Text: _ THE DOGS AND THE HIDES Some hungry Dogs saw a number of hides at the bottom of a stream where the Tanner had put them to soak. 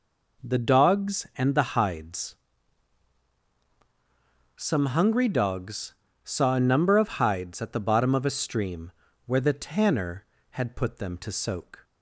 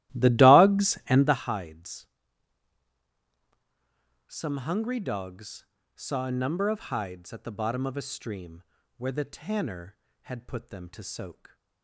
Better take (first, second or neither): first